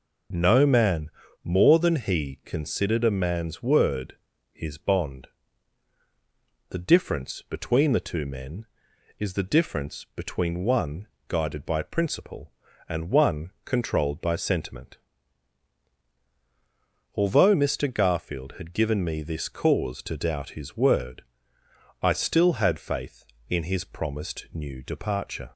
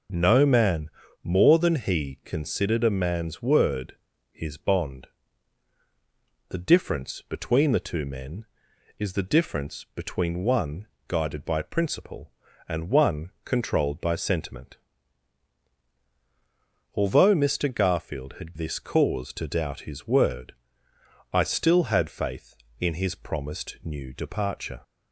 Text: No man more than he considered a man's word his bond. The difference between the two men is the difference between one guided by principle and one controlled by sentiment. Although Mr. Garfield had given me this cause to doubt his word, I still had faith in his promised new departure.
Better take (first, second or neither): first